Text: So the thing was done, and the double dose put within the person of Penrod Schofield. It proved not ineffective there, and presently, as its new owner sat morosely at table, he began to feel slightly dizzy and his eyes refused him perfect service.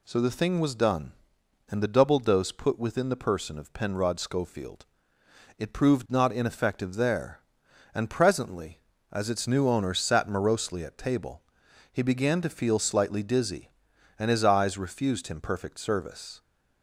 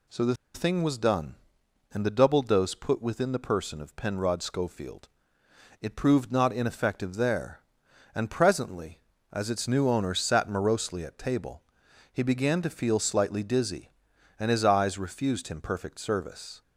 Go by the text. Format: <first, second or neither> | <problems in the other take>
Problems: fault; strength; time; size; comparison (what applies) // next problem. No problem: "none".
first | pauses between "the" and "thing"; slight; at 0.3 s; 0.19 s long